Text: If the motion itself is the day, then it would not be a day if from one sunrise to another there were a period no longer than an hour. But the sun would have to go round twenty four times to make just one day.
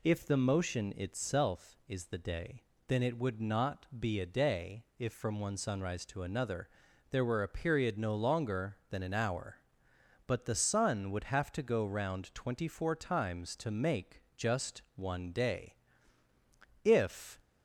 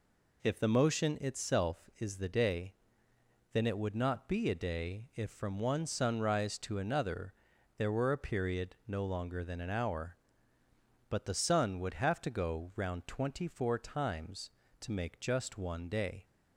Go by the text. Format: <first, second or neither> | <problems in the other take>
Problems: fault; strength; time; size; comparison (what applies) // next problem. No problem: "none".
second | pauses between "another" and "there"; at 6.6 s; 0.42 s long; also in the second // pauses between "just" and "one"; slight; at 14.8 s; 0.16 s long // goes on to say "If"; from 16.8 s on; 0.58 s long